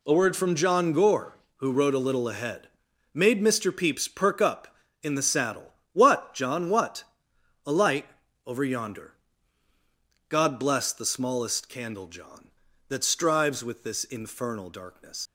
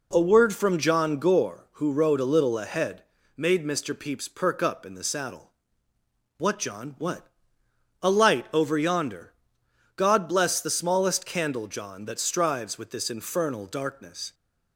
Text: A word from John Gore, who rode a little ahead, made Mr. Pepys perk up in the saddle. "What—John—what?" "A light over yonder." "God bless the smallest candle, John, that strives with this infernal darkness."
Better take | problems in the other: second | pauses between "light" and "over"; slight; at 8.0 s; 0.36 s long // leaves "darkness" unfinished; at 15.2 s; 100 ms

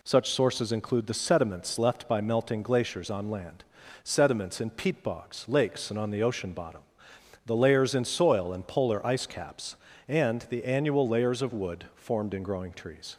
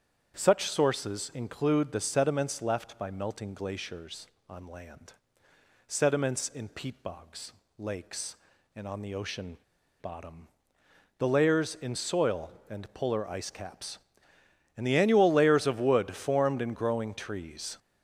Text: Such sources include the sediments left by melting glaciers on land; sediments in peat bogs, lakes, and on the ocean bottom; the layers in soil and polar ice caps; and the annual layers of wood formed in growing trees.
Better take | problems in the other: first | starts louder than the rest; strong; until 1.3 s; 8.5 dB // pauses between "ocean" and "bottom"; at 9.5 s; 0.45 s long

